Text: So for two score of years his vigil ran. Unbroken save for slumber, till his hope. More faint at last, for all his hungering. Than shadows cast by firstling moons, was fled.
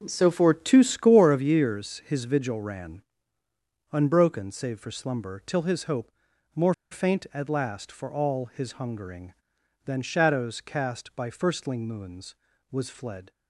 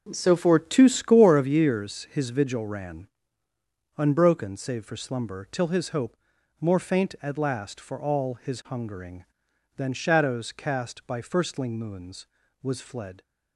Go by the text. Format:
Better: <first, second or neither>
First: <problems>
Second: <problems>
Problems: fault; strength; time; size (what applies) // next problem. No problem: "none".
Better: second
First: pauses between "More" and "faint"; slight; at 6.7 s; 0.17 s long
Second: none